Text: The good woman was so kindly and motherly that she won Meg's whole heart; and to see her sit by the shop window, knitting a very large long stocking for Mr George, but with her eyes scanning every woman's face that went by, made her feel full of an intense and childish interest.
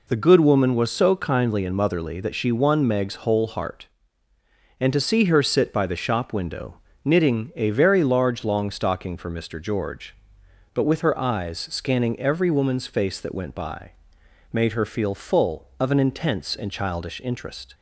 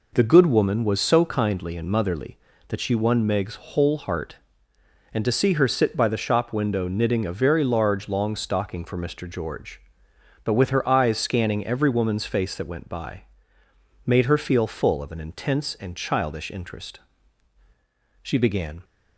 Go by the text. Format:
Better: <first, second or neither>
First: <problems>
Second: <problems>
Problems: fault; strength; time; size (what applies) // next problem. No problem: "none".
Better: first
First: none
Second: goes on to say "She began"; noticeable; from 18.2 s on; 0.62 s long